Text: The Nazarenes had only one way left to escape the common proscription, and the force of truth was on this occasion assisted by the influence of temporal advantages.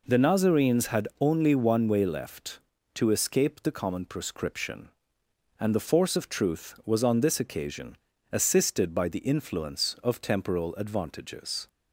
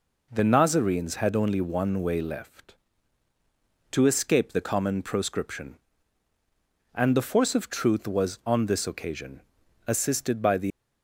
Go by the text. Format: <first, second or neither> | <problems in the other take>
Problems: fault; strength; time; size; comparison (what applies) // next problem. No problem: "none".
first | pauses between "occasion" and "assisted"; noticeable; at 9.4 s; 0.46 s long; slight in the first // stops before "influence of temporal advantages"; at 10.7 s